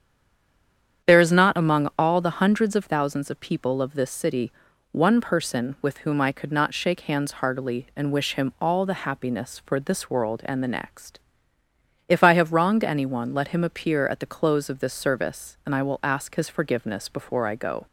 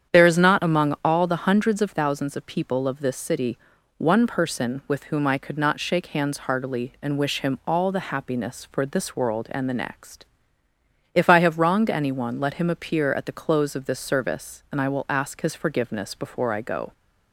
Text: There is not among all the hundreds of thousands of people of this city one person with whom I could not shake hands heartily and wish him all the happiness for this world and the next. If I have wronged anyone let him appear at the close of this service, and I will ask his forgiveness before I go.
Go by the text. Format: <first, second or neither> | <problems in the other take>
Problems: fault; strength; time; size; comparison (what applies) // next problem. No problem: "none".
second | stays silent before the first word; until 1.0 s; 1.0 s long // starts louder than the rest; strong; until 2.1 s; 8.5 dB; strong in the second // pauses between "city" and "one"; at 4.5 s; 0.40 s long; also in the second